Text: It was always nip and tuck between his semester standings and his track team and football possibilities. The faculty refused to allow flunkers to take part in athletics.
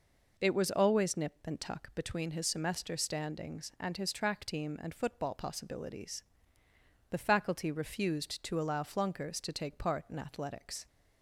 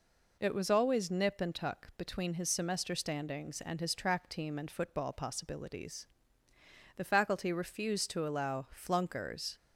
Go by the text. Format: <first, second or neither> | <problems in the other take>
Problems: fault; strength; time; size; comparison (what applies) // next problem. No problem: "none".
first | stops before "to take part in athletics"; at 9.5 s